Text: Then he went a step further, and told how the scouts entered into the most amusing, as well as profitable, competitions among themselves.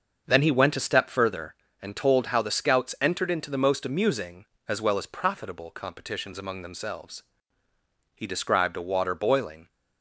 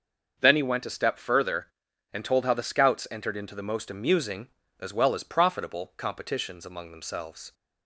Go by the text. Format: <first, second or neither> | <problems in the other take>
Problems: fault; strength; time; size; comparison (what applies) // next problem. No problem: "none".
second | starts louder than the rest; until 1.2 s; 6.5 dB; also in the second // goes on to say "He described a water boiling"; from 8.1 s on; 1.5 s long